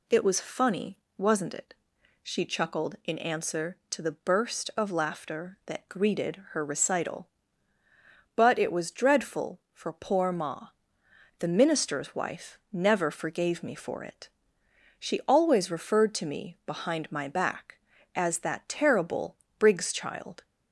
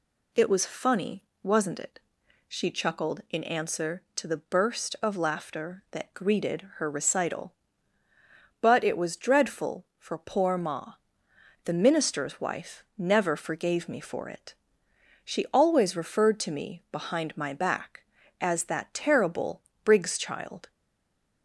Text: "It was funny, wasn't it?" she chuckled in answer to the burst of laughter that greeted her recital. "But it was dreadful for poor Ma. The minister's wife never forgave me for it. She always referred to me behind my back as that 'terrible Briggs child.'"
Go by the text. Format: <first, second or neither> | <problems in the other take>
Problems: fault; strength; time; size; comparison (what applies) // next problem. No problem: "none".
first | pauses between "terrible" and "Briggs"; slight; at 19.6 s; 0.24 s long; slight in the first // stays silent after the last word; slight; from 20.7 s on; 0.7 s long